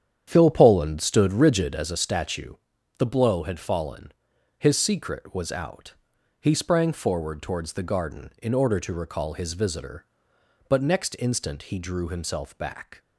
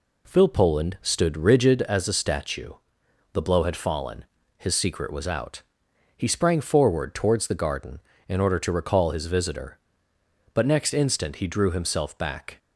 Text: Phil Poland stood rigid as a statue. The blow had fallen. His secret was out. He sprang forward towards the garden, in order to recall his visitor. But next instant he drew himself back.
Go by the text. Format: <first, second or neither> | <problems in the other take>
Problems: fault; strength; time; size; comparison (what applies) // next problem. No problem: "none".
second | starts louder than the rest; strong; until 1.9 s; 9 dB